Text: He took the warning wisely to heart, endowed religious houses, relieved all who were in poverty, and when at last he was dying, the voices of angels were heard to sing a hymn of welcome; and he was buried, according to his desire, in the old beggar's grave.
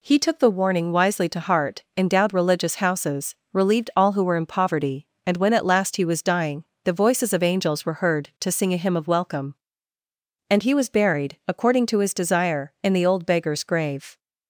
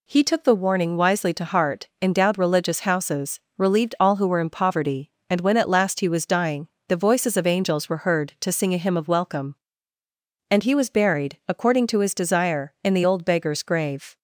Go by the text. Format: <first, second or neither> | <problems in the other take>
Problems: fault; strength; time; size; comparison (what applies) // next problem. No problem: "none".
neither | none